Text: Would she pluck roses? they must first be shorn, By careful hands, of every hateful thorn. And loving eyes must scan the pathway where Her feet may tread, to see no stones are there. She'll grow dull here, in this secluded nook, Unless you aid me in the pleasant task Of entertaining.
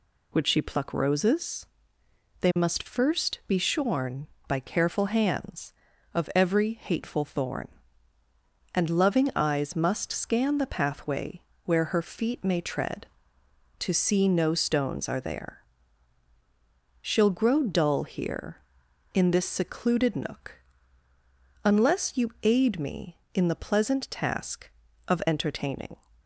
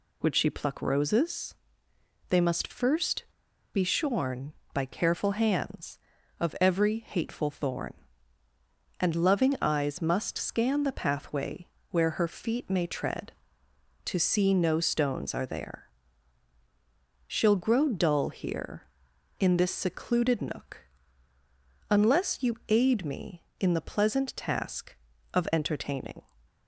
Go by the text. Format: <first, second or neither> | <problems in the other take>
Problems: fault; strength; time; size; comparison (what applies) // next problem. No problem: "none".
first | pauses between "first" and "be"; noticeable; at 3.2 s; 0.50 s long // pauses between "pathway" and "where"; slight; at 11.6 s; 0.24 s long; slight in the first